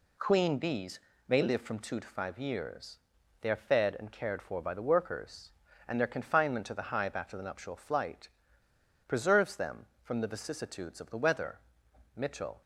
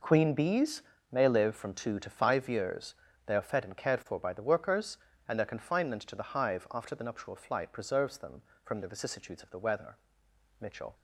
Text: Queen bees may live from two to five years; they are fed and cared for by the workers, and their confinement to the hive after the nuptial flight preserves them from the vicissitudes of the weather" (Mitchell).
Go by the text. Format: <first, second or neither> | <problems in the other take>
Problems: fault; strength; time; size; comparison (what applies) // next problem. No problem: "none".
second | pauses between "bees" and "may"; slight; at 0.9 s; 0.30 s long; slight in the second // pauses between "flight" and "preserves"; noticeable; at 8.2 s; 0.80 s long